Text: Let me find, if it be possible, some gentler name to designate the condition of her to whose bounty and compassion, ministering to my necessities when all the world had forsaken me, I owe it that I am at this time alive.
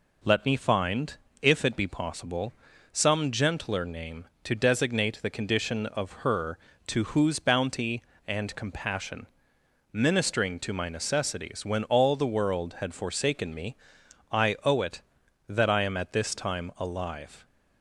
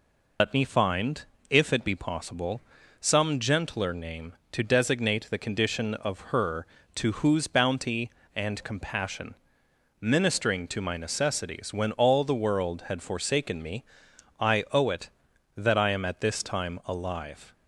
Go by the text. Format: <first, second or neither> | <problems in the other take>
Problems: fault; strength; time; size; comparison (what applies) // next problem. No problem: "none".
first | loses the start of "Let"; at 0.3 s; 85 ms